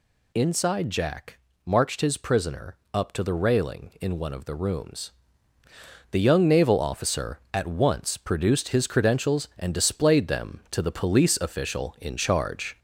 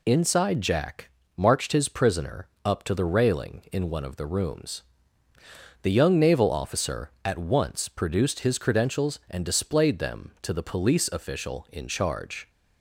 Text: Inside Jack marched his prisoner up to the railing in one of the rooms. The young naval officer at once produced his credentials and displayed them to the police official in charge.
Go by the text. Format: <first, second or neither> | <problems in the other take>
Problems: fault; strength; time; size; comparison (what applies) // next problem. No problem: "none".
second | gets louder; slight; throughout; 2.5 dB // pauses between "Jack" and "marched"; slight; at 1.3 s; 0.26 s long; slight in the second // pauses between "prisoner" and "up"; slight; at 2.7 s; 0.16 s long; slight in the second